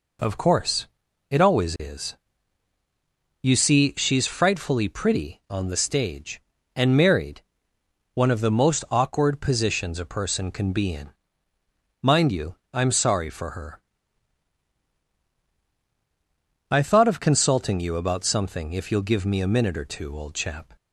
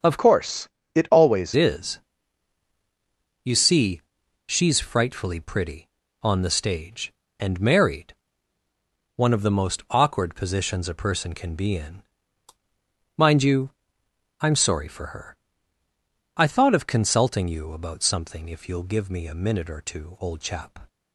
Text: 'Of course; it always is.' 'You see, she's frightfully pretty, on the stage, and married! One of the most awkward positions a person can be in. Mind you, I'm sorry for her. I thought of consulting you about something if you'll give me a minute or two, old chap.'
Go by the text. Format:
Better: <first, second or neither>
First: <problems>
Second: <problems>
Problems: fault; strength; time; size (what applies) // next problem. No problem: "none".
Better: first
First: none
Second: starts louder than the rest; strong; until 1.3 s; 7.5 dB // changes voice from "course" to "always"; from 0.1 to 1.5 s; 1.4 s long